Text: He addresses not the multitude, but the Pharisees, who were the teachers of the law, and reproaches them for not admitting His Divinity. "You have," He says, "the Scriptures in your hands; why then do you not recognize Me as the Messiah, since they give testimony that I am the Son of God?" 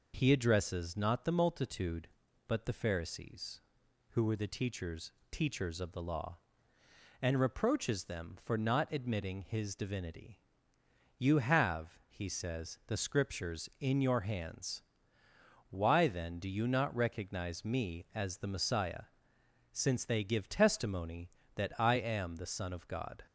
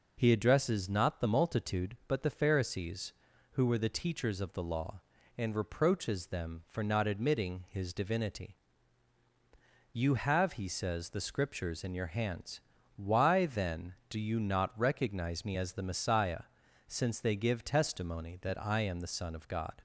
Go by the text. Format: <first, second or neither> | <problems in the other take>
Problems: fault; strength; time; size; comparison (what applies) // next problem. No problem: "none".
second | says "teachers" twice; at 5.2 s